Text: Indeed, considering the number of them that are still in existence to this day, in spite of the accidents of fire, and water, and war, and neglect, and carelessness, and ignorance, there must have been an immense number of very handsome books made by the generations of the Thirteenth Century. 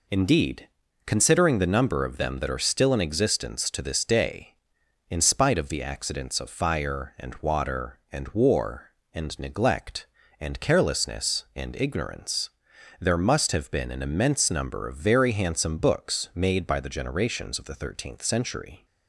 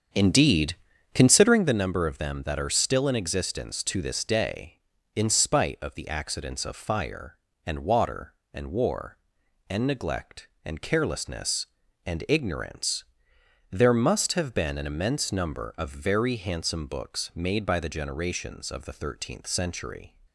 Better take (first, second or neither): first